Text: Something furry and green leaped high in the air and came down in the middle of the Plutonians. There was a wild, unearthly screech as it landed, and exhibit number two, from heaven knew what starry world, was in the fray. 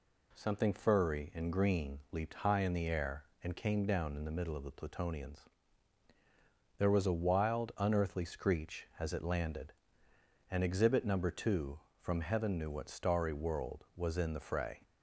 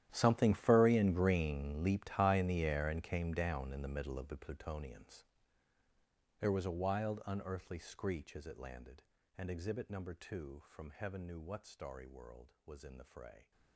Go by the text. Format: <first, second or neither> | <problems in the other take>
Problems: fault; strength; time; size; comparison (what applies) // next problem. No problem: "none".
first | gets quieter; strong; throughout; 19 dB